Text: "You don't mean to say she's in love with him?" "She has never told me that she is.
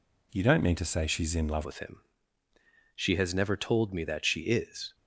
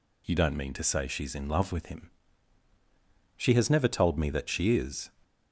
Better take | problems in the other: second | changes voice at "with"; from 1.6 s on; 3.3 s long

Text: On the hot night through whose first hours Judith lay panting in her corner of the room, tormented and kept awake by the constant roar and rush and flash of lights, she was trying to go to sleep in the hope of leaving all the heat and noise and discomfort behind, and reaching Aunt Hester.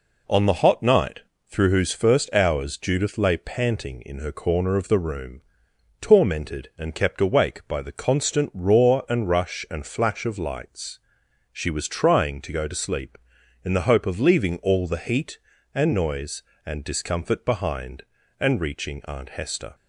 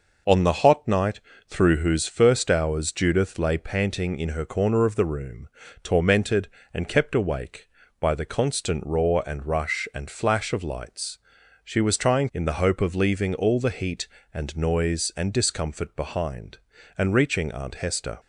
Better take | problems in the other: first | pauses between "night" and "through"; slight; at 1.2 s; 0.28 s long; slight in the first // skips "to go to sleep"; at 12.3 s

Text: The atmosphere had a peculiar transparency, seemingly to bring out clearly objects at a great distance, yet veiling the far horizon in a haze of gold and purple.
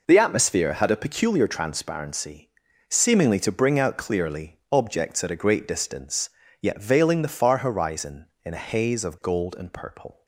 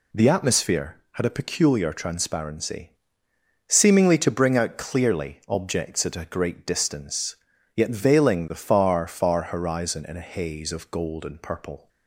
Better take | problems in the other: first | says "far" twice; at 9.0 s

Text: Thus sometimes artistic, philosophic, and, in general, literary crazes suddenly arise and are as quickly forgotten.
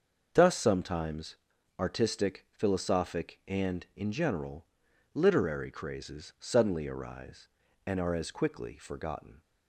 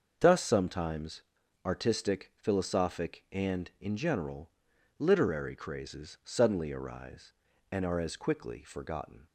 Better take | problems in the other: neither | starts louder than the rest; the same in both // pauses between "sometimes" and "artistic"; the same in both

